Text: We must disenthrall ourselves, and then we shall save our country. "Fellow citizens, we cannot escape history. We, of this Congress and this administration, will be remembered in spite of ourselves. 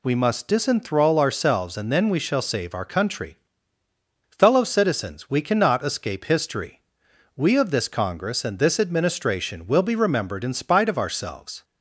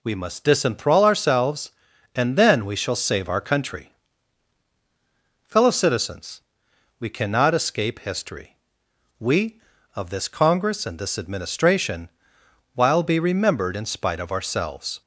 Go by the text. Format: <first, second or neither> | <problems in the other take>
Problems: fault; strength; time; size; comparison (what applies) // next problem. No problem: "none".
first | says "while" for "will"; at 12.7 s